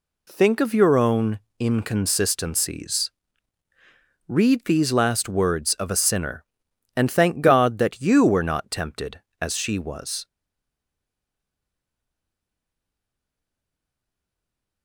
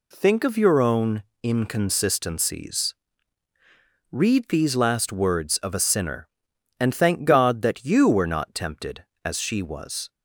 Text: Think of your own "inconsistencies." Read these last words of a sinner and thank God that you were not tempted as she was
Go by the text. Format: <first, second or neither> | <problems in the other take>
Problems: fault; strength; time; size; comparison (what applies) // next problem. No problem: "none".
second | pauses between "own" and "inconsistencies"; slight; at 1.3 s; 0.20 s long; slight in the second // stays silent after the last word; strong; from 10.2 s on; 4.6 s long